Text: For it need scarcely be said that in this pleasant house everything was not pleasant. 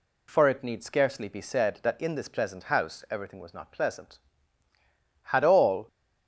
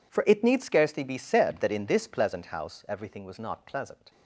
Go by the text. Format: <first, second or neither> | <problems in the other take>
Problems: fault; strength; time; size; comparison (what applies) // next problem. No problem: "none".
second | goes on to say "Had all"; noticeable; from 5.2 s on; 0.64 s long